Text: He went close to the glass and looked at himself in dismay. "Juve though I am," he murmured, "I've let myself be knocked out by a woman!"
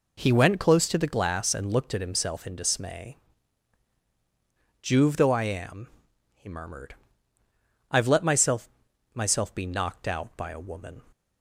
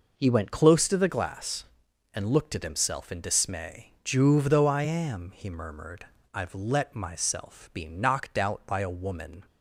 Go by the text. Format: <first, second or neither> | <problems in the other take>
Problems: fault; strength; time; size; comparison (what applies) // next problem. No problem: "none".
second | says "myself" twice; at 9.1 s